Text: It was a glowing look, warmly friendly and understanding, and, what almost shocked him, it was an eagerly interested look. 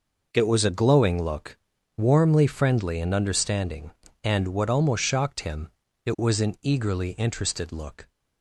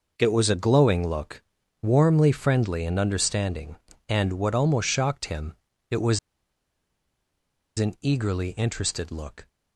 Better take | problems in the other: first | pauses between "was" and "an"; strong; at 6.1 s; 1.6 s long

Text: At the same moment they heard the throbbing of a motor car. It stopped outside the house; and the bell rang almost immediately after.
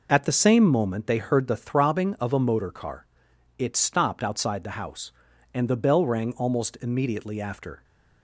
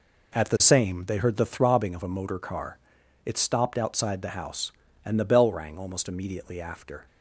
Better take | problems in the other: first | skips "moment"; at 1.0 s

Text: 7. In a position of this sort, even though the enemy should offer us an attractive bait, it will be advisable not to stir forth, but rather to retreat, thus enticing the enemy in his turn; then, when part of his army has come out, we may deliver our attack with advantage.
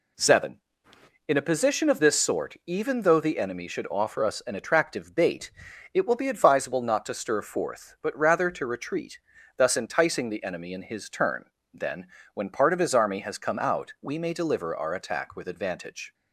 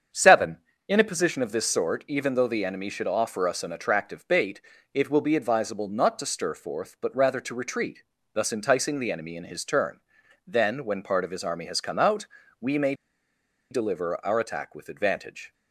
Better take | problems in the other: first | starts louder than the rest; strong; until 1.4 s; 7.5 dB // pauses between "may" and "deliver"; noticeable; at 12.9 s; 0.77 s long

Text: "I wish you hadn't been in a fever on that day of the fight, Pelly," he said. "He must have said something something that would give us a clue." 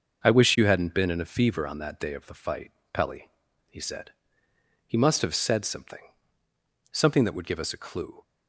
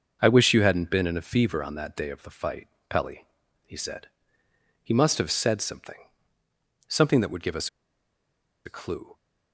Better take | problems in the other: first | pauses between "something" and "something"; noticeable; at 5.9 s; 0.96 s long; noticeable in the first // pauses between "us" and "a"; noticeable; at 7.6 s; 0.96 s long

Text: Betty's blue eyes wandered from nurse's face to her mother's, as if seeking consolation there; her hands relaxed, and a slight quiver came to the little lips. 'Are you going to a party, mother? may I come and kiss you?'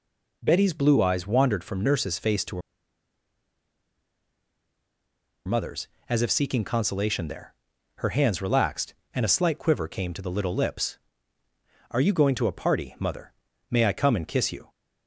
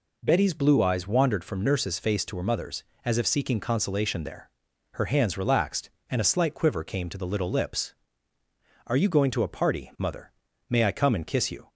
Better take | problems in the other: second | pauses between "her" and "mother's"; strong; at 2.6 s; 2.8 s long

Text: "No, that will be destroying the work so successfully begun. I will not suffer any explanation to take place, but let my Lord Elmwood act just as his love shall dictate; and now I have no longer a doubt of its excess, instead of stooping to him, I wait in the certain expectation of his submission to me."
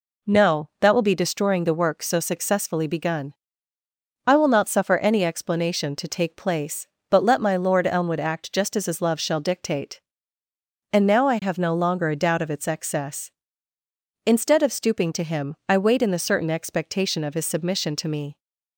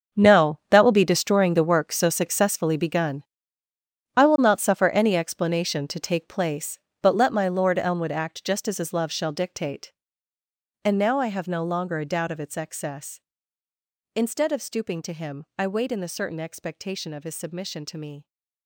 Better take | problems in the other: first | gets quieter; strong; throughout; 14 dB

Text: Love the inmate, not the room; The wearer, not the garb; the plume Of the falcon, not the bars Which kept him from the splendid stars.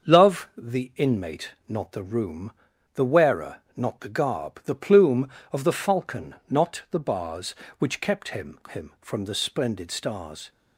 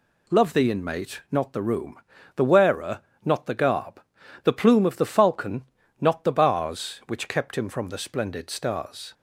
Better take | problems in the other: second | starts louder than the rest; until 1.1 s; 6.5 dB // says "him" twice; at 8.7 s

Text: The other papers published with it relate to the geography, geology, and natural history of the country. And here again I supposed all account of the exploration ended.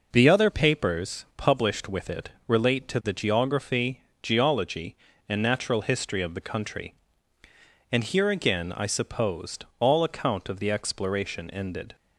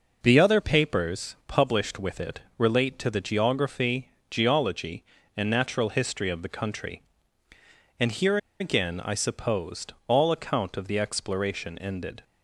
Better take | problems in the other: first | pauses between "it" and "relate"; slight; at 2.4 s; 0.18 s long; slight in the first // pauses between "here" and "again"; slight; at 8.3 s; 0.23 s long

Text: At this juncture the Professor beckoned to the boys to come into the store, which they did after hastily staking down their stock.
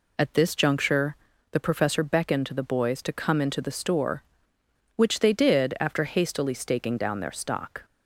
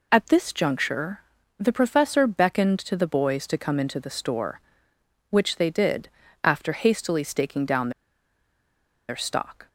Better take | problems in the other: first | pauses between "juncture" and "the"; at 1.1 s; 0.38 s long; also in the first // pauses between "did" and "after"; slight; at 6.0 s; 0.34 s long // pauses between "down" and "their"; at 7.8 s; 1.1 s long

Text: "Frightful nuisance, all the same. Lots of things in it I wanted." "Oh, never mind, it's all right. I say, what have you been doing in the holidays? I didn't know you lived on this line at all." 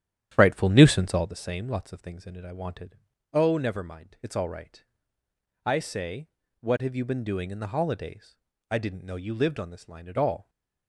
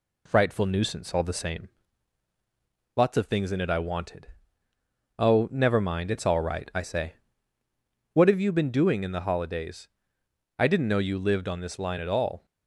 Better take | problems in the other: second | starts louder than the rest; strong; until 1.4 s; 10 dB

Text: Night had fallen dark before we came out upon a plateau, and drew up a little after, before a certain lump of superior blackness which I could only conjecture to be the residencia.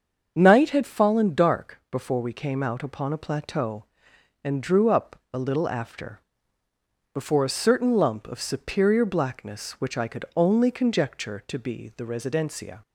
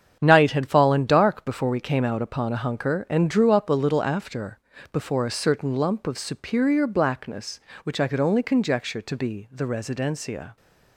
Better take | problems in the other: first | starts louder than the rest; strong; until 1.2 s; 8 dB; also in the first // says "hunker" for "plateau"; at 2.6 s

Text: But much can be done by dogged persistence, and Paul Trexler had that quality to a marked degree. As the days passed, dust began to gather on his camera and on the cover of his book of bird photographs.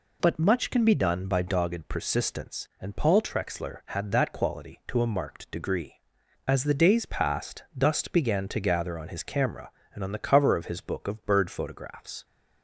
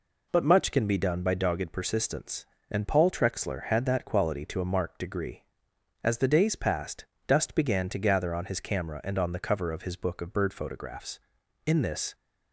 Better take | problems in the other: first | goes on to say "In this"; slight; from 11.6 s on; 0.48 s long

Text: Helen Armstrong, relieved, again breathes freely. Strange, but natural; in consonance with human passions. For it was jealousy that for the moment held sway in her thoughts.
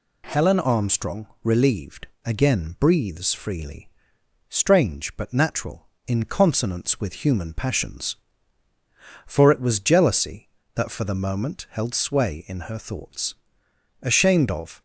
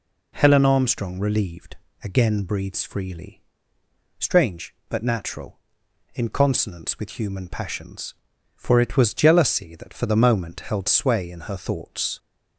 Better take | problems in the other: second | goes on to say "Ashamed of"; noticeable; from 14.0 s on; 0.80 s long

